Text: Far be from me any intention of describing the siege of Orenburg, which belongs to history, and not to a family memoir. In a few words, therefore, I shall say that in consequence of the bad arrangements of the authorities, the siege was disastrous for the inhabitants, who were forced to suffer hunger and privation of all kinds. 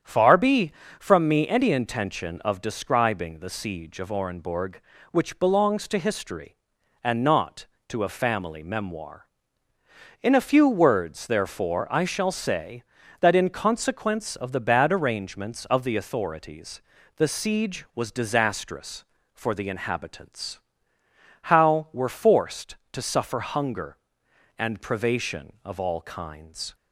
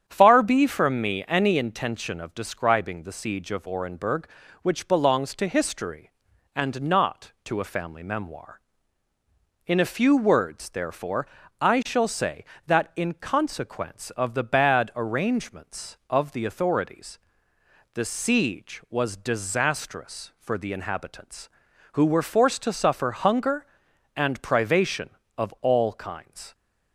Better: second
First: starts louder than the rest; strong; until 1.2 s; 8.5 dB // says "how" for "who"; at 21.4 s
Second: starts louder than the rest; strong; until 1.0 s; 8.5 dB

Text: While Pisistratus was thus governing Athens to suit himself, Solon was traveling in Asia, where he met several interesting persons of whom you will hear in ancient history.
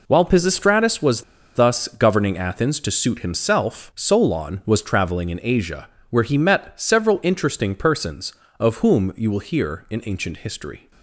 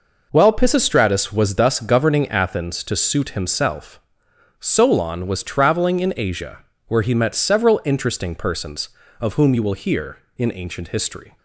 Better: second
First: pauses between "was" and "thus"; slight; at 1.2 s; 0.32 s long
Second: none

